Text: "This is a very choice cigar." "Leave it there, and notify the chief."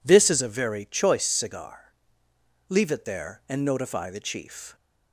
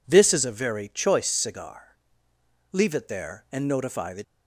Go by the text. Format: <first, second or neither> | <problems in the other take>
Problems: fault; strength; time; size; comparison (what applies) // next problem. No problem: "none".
first | stops before "chief"; at 4.2 s